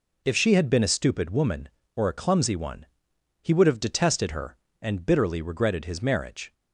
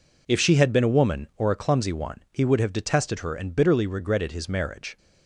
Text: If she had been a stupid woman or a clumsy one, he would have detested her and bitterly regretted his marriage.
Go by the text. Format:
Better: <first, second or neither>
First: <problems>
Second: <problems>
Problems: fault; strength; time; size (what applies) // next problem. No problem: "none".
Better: first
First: none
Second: skips "stupid"; at 0.9 s